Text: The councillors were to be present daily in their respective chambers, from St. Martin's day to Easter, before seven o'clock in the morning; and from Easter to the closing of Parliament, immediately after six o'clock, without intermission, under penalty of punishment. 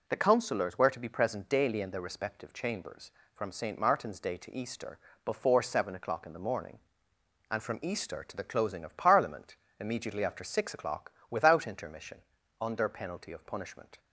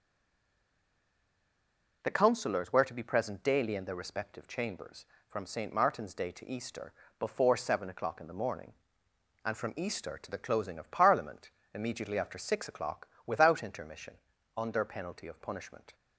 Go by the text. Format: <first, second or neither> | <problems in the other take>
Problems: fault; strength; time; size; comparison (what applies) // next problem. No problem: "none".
first | stays silent before the first word; noticeable; until 2.0 s; 2.0 s long